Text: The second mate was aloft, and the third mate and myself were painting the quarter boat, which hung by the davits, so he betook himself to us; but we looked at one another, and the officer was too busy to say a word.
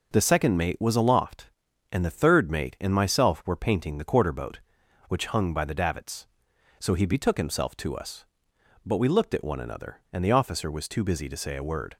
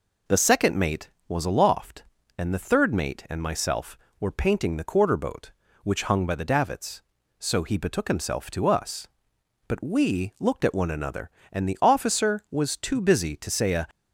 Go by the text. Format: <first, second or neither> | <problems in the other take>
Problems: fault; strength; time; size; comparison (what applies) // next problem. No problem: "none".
first | stops before "word"; at 13.9 s